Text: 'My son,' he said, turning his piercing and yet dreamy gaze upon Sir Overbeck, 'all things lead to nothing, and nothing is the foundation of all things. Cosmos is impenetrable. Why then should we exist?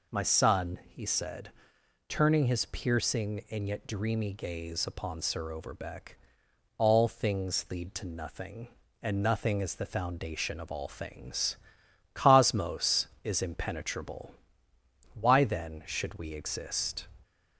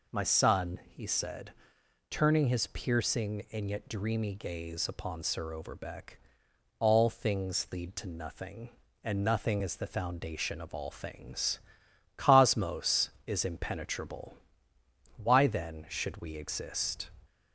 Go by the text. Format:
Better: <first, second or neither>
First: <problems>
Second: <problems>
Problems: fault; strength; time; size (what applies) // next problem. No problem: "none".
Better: neither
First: none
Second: none